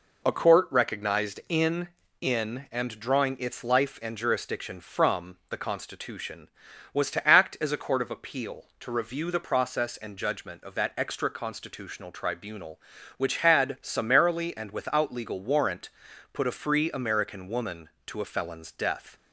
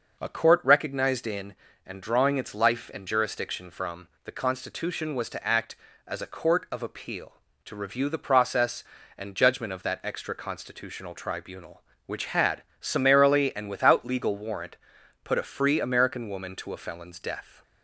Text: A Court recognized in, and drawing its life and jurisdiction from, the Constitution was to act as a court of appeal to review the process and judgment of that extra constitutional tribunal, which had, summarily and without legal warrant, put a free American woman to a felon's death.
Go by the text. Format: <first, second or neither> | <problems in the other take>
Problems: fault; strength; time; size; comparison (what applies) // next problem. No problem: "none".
second | says "in" twice; at 2.2 s